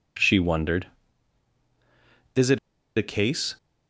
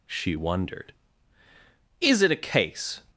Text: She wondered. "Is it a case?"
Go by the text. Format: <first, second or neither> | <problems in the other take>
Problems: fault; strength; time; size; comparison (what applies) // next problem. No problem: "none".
second | pauses between "it" and "a"; at 2.5 s; 0.38 s long